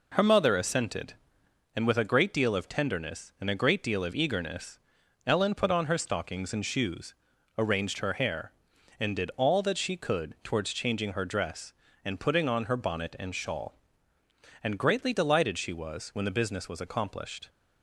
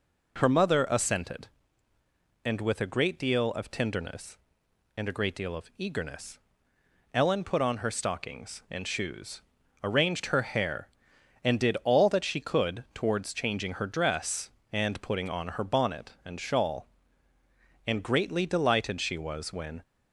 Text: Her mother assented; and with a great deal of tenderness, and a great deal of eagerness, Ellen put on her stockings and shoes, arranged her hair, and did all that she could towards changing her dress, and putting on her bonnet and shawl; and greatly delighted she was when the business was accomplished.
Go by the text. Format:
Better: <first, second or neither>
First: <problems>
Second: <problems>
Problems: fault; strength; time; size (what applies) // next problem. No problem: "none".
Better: first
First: none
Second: stops before "the business was accomplished"; at 19.8 s